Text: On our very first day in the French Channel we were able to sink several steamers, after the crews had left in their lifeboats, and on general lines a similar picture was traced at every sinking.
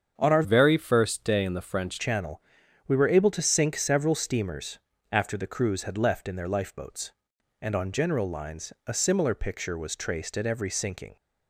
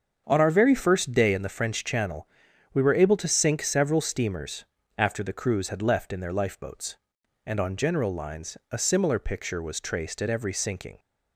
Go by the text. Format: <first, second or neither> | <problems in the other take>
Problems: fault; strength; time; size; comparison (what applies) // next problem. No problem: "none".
second | starts louder than the rest; strong; until 1.1 s; 7.5 dB; also in the second // changes voice from "very" to "French"; from 0.4 to 1.9 s; 1.5 s long // pauses between "Channel" and "we"; noticeable; at 2.4 s; 0.46 s long; noticeable in the second